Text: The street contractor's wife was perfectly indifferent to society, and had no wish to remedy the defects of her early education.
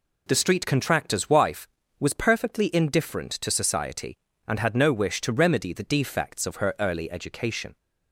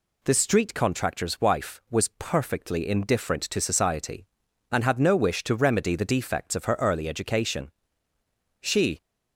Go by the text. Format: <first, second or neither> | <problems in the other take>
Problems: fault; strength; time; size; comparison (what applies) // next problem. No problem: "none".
first | goes on to say "She"; slight; from 8.5 s on; 0.42 s long